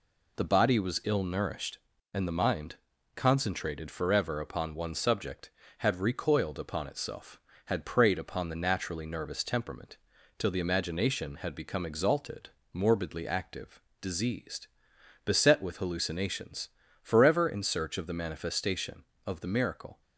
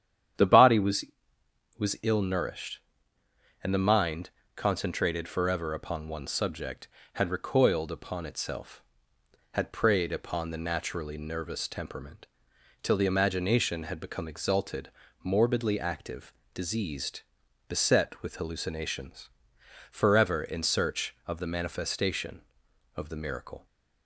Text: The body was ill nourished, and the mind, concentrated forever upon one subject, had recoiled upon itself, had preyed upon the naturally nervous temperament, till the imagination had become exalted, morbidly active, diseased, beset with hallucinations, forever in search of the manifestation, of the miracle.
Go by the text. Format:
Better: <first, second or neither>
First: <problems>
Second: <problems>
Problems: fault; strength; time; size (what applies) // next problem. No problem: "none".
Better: first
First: none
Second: starts louder than the rest; strong; until 2.2 s; 9.5 dB // says "was" twice; at 1.7 s